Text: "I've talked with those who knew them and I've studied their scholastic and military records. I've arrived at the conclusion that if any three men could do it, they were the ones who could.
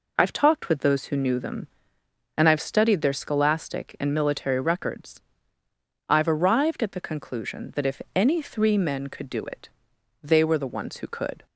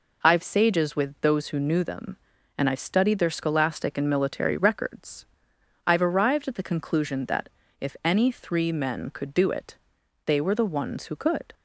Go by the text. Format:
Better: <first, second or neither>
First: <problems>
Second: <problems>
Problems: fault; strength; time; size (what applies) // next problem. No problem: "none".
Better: first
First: none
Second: says "sages" for "talked"; at 0.4 s // pauses between "that" and "if"; slight; at 7.4 s; 0.30 s long